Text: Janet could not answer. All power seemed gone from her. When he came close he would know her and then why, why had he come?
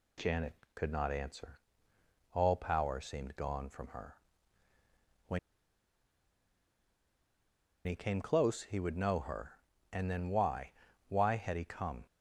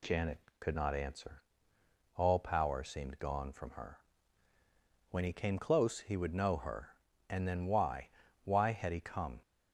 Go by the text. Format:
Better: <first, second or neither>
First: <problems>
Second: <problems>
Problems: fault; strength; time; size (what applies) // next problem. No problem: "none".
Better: second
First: pauses between "When" and "he"; strong; at 5.3 s; 2.4 s long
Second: none